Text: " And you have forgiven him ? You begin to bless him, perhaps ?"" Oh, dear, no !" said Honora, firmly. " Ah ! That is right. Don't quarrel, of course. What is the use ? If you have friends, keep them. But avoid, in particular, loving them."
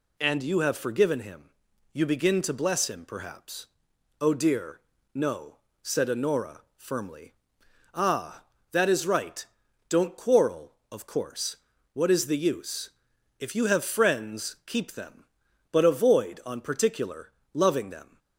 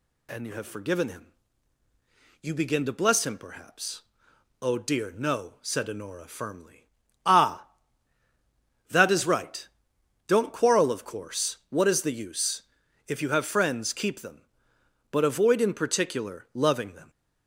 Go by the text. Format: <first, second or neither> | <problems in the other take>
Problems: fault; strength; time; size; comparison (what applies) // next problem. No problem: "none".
second | says "on" for "in"; at 16.4 s